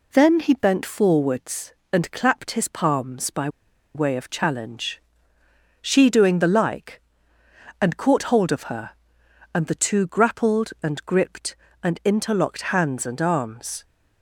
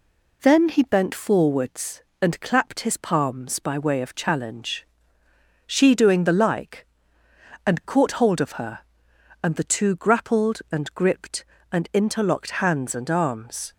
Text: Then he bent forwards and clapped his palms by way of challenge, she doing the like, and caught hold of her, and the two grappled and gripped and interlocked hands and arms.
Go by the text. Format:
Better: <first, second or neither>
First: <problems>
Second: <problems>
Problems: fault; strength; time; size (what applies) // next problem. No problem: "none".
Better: second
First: pauses between "by" and "way"; noticeable; at 3.4 s; 0.46 s long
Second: none